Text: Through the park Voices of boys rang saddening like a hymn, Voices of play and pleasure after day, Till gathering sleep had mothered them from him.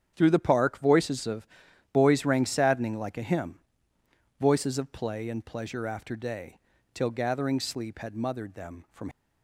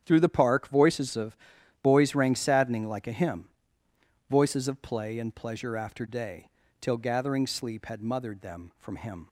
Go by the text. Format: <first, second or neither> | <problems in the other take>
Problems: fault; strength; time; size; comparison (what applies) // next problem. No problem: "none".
second | starts louder than the rest; strong; until 1.1 s; 8.5 dB; strong in the second // pauses between "of" and "boys"; at 1.4 s; 0.44 s long; also in the second // stops before "him"; at 9.1 s